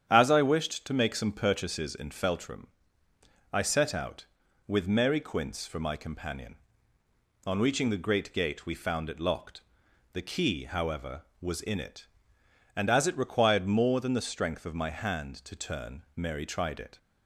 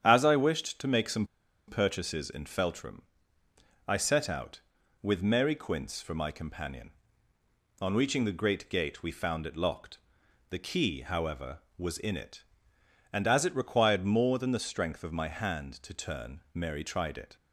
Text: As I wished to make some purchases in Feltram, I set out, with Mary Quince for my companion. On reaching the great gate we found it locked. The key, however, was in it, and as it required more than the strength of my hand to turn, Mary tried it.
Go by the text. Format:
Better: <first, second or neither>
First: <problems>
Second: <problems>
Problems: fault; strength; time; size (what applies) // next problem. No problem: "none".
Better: first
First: starts louder than the rest; strong; until 1.0 s; 9 dB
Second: starts louder than the rest; strong; until 1.0 s; 9 dB // pauses between "some" and "purchases"; at 1.2 s; 0.40 s long